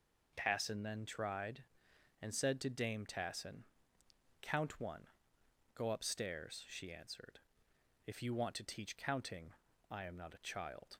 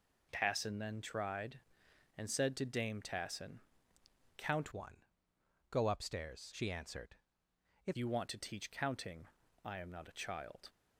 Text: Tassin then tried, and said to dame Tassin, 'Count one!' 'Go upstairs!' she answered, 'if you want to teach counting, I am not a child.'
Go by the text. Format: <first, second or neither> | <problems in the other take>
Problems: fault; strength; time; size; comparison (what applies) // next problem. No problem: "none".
first | changes voice from "one" to "if"; from 4.7 to 7.9 s; 3.2 s long